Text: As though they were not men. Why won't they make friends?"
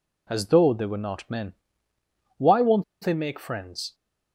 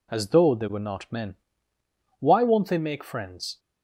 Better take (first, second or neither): second